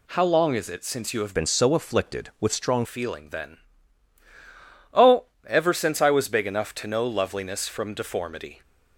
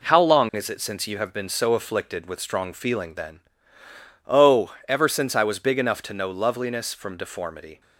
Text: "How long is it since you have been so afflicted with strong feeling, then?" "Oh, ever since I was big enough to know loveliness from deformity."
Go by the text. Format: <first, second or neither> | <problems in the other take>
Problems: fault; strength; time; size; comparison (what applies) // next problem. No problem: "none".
second | changes voice from "been" to "strong"; from 1.3 to 2.8 s; 1.5 s long